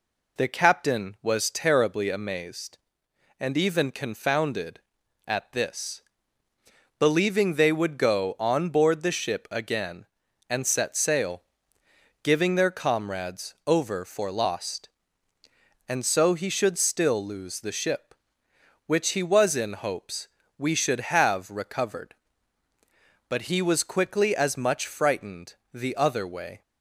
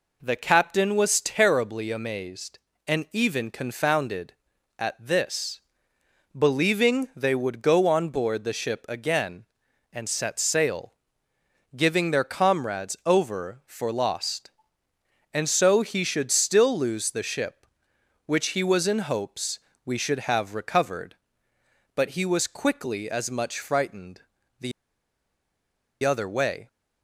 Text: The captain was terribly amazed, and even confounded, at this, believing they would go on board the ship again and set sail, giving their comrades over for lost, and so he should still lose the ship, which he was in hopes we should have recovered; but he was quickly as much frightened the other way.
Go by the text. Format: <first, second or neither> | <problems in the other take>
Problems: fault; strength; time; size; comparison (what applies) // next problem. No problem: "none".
first | pauses between "hopes" and "we"; slight; at 19.5 s; 0.24 s long; slight in the first // pauses between "frightened" and "the"; slight; at 24.2 s; 0.36 s long; slight in the first // pauses between "the" and "other"; strong; at 24.7 s; 1.3 s long